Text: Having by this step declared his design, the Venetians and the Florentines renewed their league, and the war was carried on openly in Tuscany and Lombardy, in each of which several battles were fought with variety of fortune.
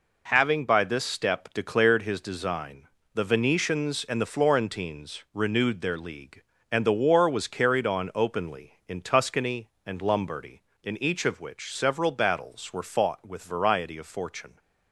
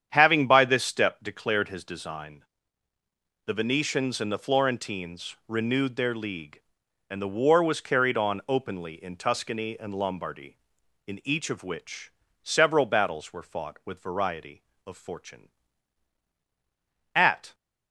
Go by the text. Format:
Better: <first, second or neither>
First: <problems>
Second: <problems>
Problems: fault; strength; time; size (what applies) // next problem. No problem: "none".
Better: first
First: none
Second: starts louder than the rest; strong; until 1.1 s; 8.5 dB // pauses between "which" and "several"; slight; at 12.1 s; 0.30 s long // goes on to say "At"; slight; from 17.1 s on; 0.40 s long